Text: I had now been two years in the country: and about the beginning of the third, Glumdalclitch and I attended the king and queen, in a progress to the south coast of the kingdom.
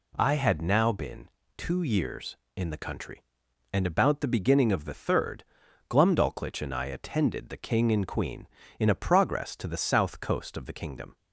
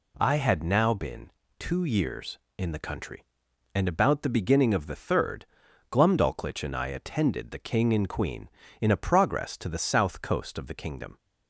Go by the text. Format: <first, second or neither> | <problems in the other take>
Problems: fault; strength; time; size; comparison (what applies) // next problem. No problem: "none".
neither | pauses between "been" and "two"; slight; the same in both